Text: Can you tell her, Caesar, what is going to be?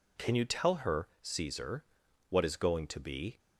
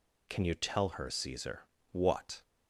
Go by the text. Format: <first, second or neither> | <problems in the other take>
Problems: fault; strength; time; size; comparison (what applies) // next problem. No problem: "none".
first | stops before "is going to be"; at 2.4 s